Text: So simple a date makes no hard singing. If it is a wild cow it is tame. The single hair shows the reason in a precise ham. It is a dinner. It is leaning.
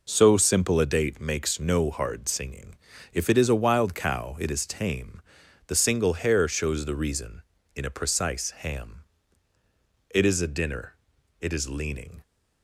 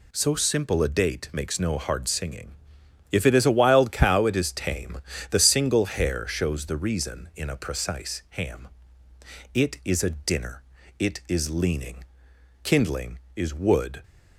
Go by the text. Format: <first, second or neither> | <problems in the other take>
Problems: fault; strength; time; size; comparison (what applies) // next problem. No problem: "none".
first | goes on to say "Kindling is wood"; from 12.6 s on; 1.3 s long